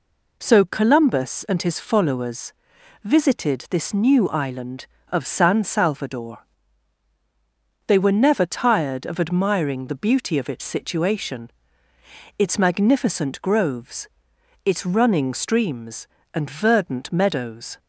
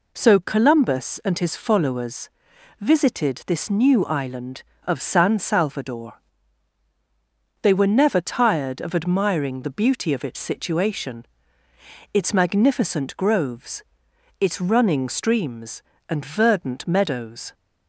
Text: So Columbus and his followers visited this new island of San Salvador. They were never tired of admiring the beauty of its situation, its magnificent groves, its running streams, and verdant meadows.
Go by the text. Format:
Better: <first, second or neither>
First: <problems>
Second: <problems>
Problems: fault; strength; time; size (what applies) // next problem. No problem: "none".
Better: neither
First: pauses between "followers" and "visited"; noticeable; at 2.5 s; 0.50 s long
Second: pauses between "followers" and "visited"; noticeable; at 2.2 s; 0.50 s long